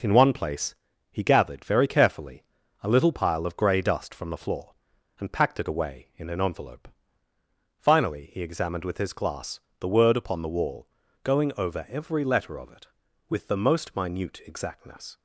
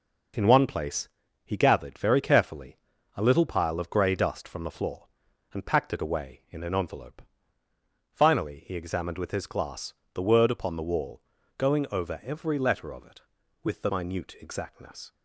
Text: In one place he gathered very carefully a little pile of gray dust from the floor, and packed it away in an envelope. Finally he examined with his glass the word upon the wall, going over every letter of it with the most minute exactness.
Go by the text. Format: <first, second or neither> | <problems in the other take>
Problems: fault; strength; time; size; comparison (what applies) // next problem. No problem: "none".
first | pauses between "place" and "he"; at 1.0 s; 0.38 s long; also in the first // pauses between "carefully" and "a"; at 2.7 s; 0.40 s long; also in the first // pauses between "glass" and "the"; slight; at 9.9 s; 0.22 s long; slight in the first // skips "most"; at 13.8 s